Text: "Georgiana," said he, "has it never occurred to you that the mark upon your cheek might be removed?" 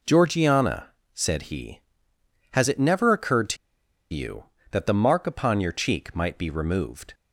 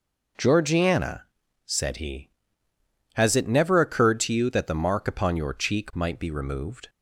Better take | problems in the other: second | pauses between "to" and "you"; noticeable; at 3.5 s; 0.57 s long

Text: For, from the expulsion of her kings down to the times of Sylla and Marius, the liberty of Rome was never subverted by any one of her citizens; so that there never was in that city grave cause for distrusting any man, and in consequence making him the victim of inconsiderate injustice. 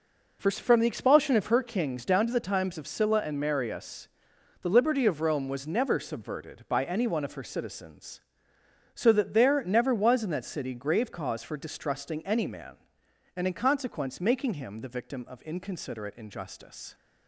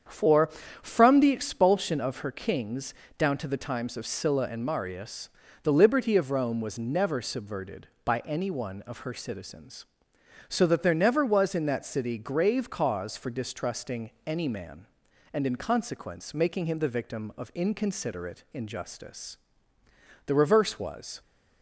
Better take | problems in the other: first | starts louder than the rest; strong; until 1.3 s; 8 dB // pauses between "kings" and "down"; slight; at 2.9 s; 0.24 s long // goes on to say "The reverse was"; noticeable; from 20.2 s on; 0.94 s long

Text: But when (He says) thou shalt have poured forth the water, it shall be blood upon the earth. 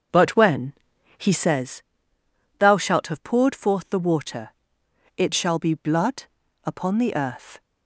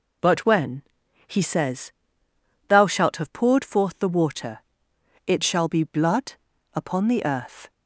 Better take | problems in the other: second | starts louder than the rest; until 1.6 s; 6.5 dB // pauses between "blood" and "upon"; at 6.2 s; 0.42 s long; also in the second

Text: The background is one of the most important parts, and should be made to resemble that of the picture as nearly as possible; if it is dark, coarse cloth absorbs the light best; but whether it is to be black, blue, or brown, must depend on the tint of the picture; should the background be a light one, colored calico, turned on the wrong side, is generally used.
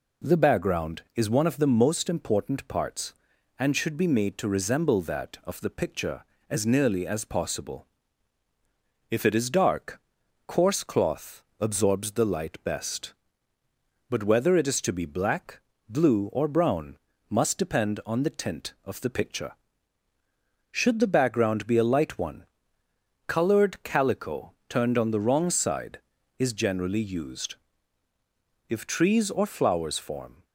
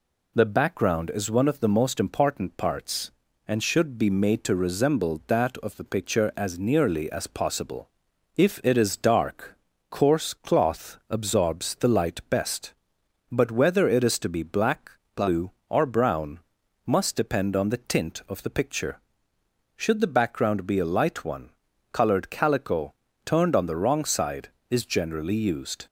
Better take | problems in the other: second | pauses between "cloth" and "absorbs"; slight; at 11.4 s; 0.16 s long // goes on to say "If trees or flowers form"; strong; from 28.6 s on; 1.7 s long

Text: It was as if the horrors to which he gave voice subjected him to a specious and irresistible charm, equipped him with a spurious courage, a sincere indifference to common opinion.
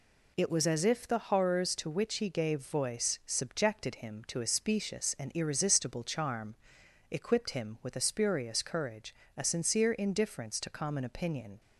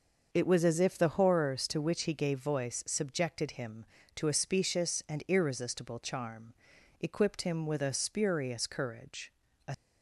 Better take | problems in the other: first | starts louder than the rest; noticeable; until 1.3 s; 6 dB // stops before "sincere indifference to common opinion"; at 9.7 s

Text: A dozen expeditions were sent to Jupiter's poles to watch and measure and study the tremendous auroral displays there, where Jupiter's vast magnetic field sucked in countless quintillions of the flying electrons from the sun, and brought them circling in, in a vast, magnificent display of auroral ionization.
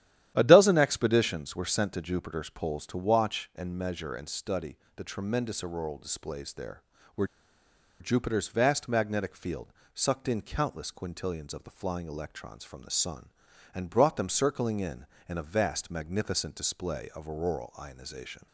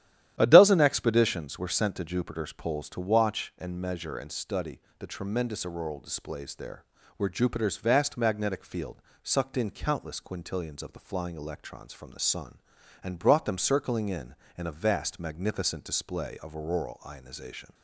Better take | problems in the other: second | starts louder than the rest; strong; until 1.3 s; 12 dB; strong in the second // pauses between "study" and "the"; slight; at 4.7 s; 0.18 s long; slight in the second // pauses between "where" and "Jupiter's"; noticeable; at 7.2 s; 0.73 s long // pauses between "field" and "sucked"; slight; at 9.7 s; 0.22 s long; slight in the second

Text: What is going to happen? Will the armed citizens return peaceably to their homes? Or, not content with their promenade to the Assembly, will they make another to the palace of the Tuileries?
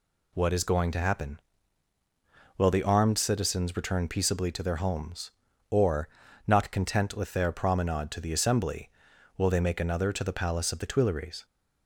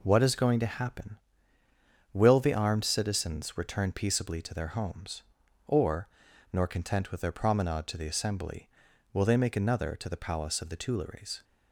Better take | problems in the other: first | says "nor" for "not"; at 6.5 s

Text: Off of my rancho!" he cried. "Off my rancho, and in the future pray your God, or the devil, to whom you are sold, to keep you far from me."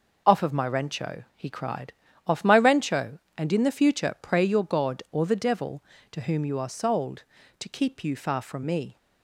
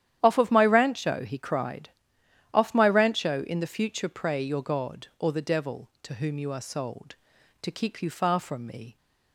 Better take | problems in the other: first | starts louder than the rest; strong; until 1.2 s; 10.5 dB // skips "and"; at 3.4 s

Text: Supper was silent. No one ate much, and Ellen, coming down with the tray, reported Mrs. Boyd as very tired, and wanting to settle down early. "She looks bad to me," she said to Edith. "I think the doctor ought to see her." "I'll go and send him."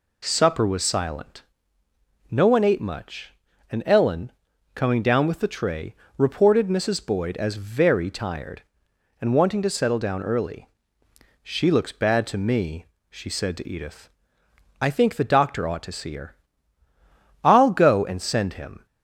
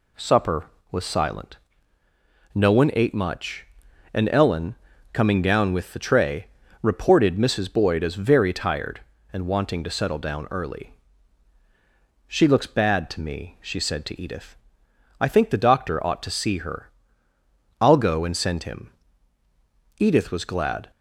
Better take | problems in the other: first | goes on to say "Edith was glad"; noticeable; from 19.9 s on; 0.92 s long

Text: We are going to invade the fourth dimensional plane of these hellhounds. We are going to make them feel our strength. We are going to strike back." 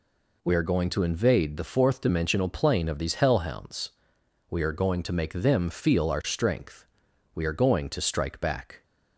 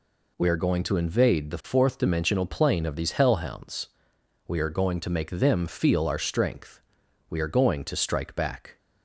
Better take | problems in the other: neither | none

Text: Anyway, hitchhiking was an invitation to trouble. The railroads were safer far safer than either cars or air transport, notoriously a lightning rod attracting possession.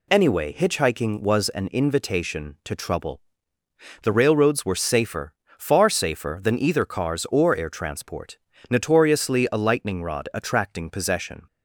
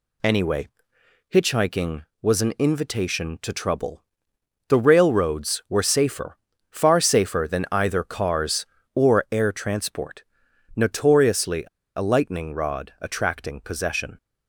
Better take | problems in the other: first | pauses between "safer" and "far"; slight; at 6.3 s; 0.34 s long; slight in the first // pauses between "notoriously" and "a"; slight; at 11.6 s; 0.32 s long

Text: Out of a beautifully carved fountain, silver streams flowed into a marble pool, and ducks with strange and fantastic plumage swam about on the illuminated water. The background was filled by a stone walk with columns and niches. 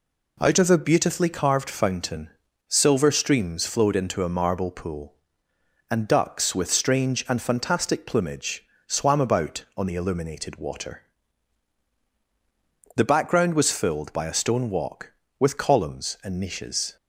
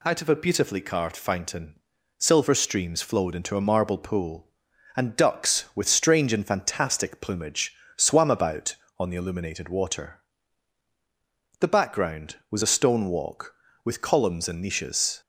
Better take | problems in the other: first | pauses between "plumage" and "swam"; slight; at 7.7 s; 0.24 s long; slight in the first // skips "filled by"; at 12.6 s

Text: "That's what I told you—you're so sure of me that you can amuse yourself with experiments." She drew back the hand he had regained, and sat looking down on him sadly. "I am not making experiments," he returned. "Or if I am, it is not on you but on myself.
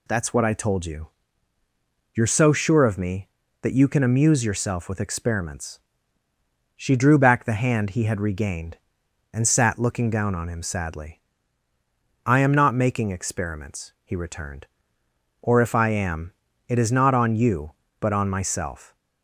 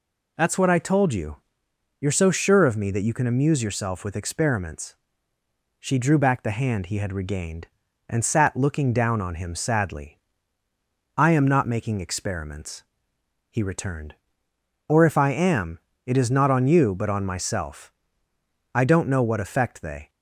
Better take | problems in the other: first | goes on to say "I don't know what effect they"; from 18.7 s on; 1.3 s long

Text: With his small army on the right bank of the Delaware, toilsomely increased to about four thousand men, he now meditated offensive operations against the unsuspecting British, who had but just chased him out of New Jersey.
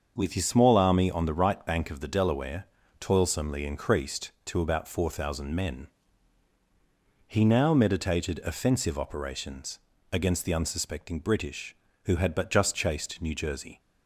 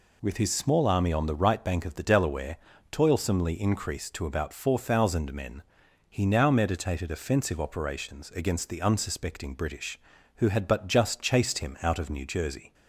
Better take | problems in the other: second | starts louder than the rest; until 1.1 s; 6.5 dB // pauses between "operations" and "against"; slight; at 9.7 s; 0.32 s long // skips "him out of"; at 13.2 s

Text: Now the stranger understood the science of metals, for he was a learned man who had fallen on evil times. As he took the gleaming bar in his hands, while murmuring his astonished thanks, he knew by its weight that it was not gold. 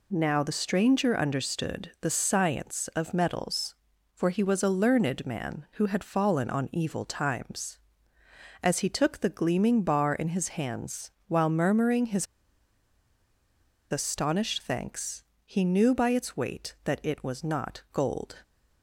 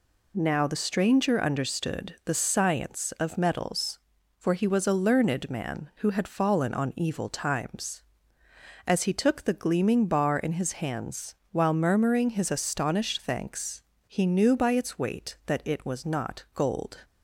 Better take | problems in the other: second | pauses between "his" and "astonished"; strong; at 12.2 s; 1.6 s long

